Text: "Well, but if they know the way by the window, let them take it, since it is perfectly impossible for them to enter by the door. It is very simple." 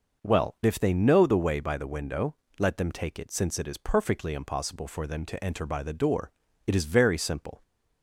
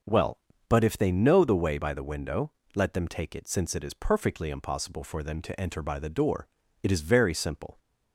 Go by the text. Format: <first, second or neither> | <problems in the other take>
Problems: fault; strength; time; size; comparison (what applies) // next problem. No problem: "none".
second | skips "but"; at 0.5 s